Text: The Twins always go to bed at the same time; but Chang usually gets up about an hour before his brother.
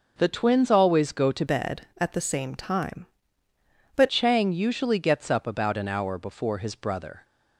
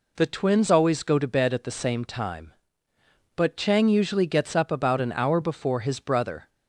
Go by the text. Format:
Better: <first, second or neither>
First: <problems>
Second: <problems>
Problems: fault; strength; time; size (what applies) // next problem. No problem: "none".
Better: second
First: changes voice from "bed" to "but"; from 1.4 to 4.0 s; 2.6 s long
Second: none